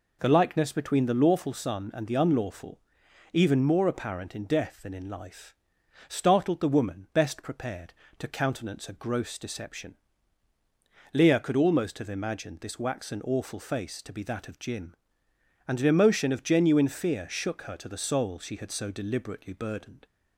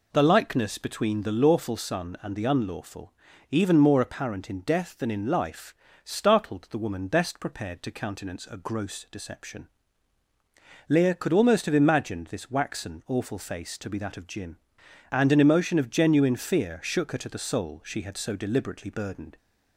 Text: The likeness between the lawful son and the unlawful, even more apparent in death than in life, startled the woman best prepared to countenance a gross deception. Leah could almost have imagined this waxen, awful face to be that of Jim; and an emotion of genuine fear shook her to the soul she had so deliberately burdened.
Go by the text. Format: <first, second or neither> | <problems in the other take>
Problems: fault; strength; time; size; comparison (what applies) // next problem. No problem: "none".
neither | none